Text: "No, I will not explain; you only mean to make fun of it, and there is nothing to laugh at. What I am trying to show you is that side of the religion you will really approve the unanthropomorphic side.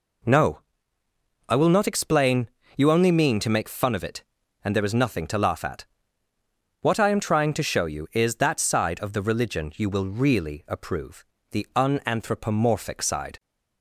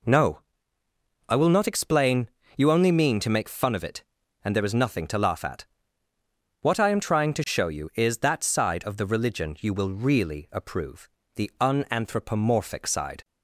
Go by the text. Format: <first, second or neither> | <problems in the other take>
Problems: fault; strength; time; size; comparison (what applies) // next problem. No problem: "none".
neither | pauses between "approve" and "the"; slight; the same in both